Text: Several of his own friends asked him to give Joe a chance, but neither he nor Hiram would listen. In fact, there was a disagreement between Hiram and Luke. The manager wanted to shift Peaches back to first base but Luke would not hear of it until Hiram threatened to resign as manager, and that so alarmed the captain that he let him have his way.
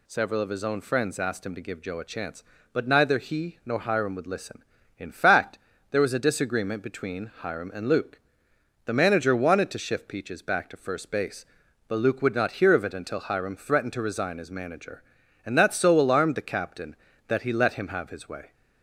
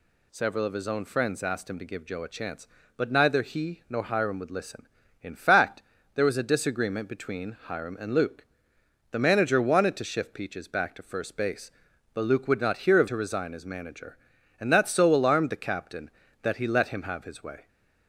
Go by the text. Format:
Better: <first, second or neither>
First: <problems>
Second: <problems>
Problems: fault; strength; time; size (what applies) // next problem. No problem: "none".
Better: first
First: none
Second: skips "it until Hiram threatened"; at 13.0 s